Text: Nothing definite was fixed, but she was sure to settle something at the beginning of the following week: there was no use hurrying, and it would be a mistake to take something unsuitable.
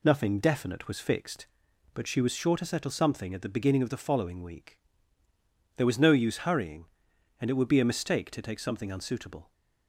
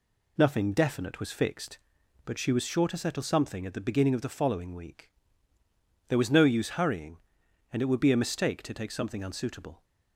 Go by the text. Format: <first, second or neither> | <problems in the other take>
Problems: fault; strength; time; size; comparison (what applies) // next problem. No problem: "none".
neither | none